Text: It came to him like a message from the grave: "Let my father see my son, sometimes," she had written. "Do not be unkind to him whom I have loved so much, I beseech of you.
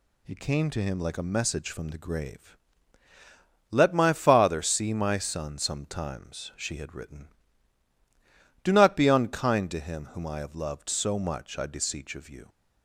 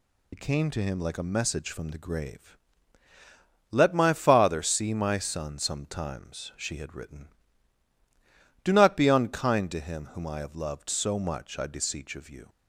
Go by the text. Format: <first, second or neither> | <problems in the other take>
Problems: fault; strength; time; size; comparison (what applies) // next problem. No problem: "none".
first | loses the start of "It"; at 0.3 s; 55 ms